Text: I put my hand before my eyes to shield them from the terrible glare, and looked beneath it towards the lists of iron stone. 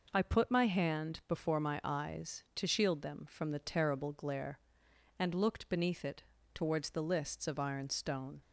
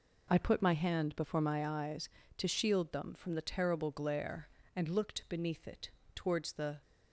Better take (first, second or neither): first